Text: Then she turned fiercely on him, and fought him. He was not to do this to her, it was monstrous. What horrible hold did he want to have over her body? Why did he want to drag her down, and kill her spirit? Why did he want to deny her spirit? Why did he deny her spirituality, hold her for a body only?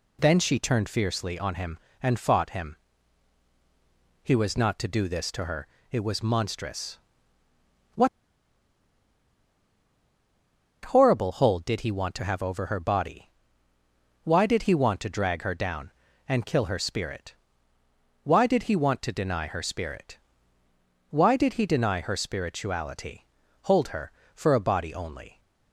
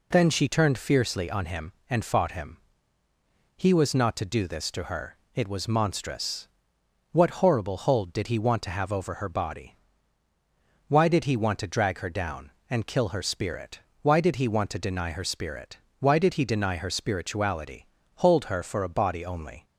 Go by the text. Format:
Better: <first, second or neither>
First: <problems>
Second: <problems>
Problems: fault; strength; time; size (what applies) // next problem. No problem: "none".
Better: second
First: pauses between "What" and "horrible"; strong; at 8.0 s; 2.7 s long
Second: none